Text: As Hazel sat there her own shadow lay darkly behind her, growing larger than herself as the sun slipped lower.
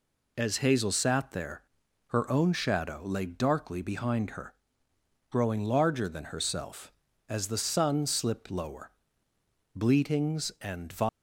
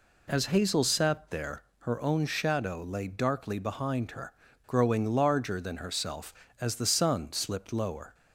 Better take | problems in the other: second | pauses between "there" and "her"; at 1.6 s; 0.44 s long; slight in the second // goes on to say "Bleatings and"; noticeable; from 9.7 s on; 1.1 s long

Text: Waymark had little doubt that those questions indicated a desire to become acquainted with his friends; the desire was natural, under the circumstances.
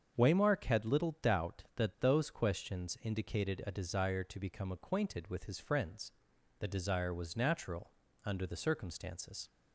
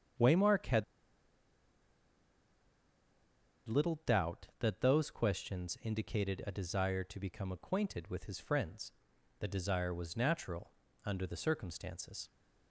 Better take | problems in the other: first | starts louder than the rest; strong; until 4.0 s; 7 dB; strong in the first // pauses between "had" and "little"; strong; at 0.8 s; 2.8 s long

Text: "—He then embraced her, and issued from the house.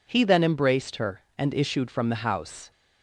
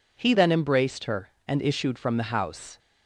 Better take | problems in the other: neither | none

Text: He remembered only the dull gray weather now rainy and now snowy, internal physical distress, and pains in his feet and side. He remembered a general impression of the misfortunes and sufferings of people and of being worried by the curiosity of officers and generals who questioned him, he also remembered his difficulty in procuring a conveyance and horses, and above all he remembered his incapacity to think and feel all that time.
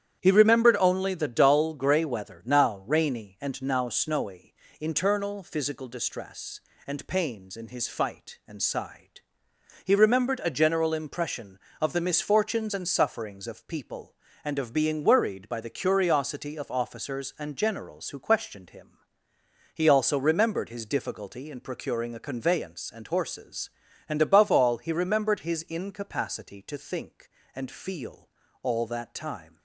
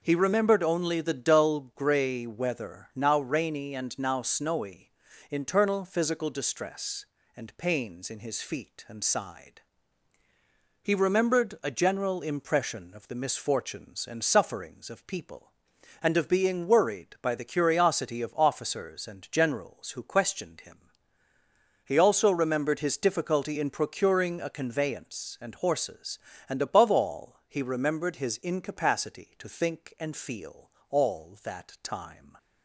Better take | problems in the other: second | starts louder than the rest; strong; until 1.2 s; 10 dB // says "fight" for "feet"; at 7.8 s // pauses between "feel" and "all"; slight; at 28.2 s; 0.34 s long; slight in the second

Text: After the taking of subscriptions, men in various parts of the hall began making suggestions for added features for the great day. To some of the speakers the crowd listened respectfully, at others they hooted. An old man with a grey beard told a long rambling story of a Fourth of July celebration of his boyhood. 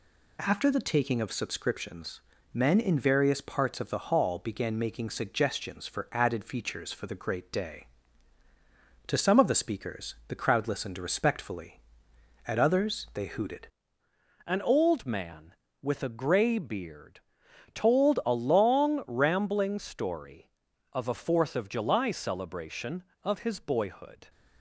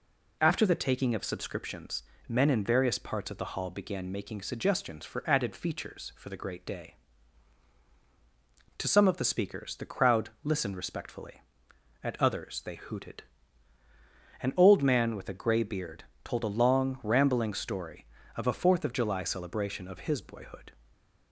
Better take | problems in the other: second | changes voice at "An"; from 14.4 s on; 9.8 s long // pauses between "beard" and "told"; noticeable; at 17.1 s; 0.54 s long; slight in the second

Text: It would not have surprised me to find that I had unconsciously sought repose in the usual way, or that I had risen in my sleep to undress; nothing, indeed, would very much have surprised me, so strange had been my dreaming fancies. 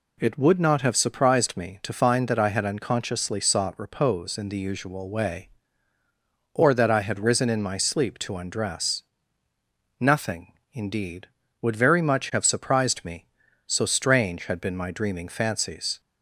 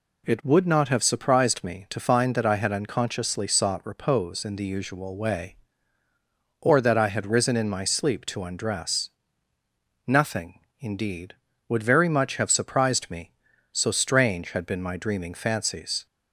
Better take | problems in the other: neither | none

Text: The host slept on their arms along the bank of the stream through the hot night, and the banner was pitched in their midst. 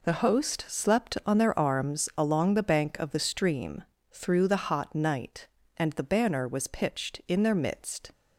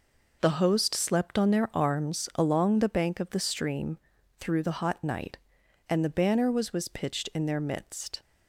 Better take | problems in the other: first | pauses between "stream" and "through"; at 3.9 s; 0.42 s long; slight in the first // says "was" twice; at 6.7 s

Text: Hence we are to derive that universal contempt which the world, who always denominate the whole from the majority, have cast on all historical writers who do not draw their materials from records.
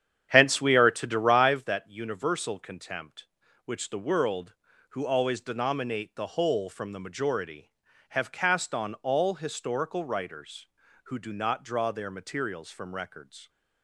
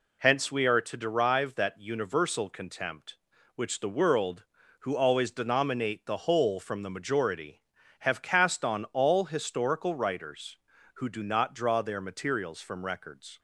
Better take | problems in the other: second | starts louder than the rest; strong; until 1.7 s; 9 dB

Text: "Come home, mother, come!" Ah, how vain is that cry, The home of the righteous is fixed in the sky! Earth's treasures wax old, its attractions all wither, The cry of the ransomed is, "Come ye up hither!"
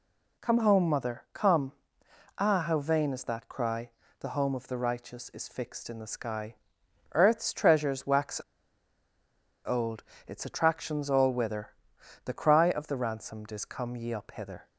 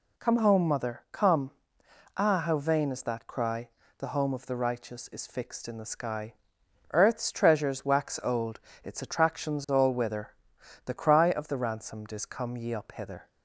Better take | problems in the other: second | pauses between "wax" and "old"; strong; at 8.3 s; 1.2 s long

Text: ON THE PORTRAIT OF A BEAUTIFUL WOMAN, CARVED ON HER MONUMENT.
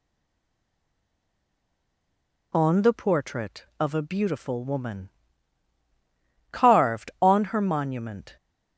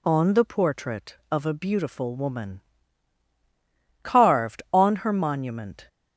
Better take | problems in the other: second | stays silent before the first word; until 2.5 s; 2.5 s long

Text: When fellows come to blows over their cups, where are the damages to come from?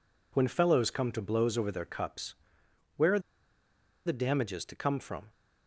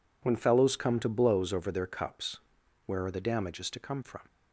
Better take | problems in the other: second | pauses between "are" and "the"; noticeable; at 3.1 s; 0.86 s long

